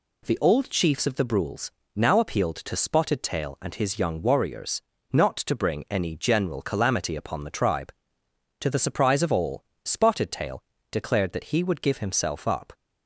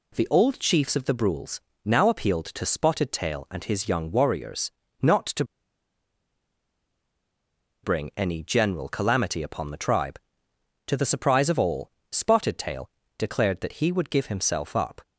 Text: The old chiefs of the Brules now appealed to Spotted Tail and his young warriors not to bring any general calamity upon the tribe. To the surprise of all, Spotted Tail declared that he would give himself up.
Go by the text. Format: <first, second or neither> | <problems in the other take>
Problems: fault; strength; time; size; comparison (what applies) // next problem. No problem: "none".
first | pauses between "Brules" and "now"; slight; at 1.5 s; 0.24 s long; slight in the first // pauses between "warriors" and "not"; slight; at 4.6 s; 0.32 s long; slight in the first // pauses between "to" and "bring"; strong; at 5.4 s; 2.3 s long // pauses between "Tail" and "declared"; slight; at 12.9 s; 0.28 s long; slight in the first